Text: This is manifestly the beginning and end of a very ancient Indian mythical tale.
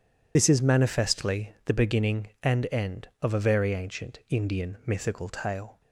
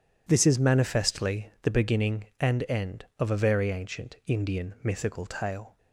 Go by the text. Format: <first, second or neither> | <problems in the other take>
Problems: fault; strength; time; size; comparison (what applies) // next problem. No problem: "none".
second | loses the start of "This"; at 0.3 s; 50 ms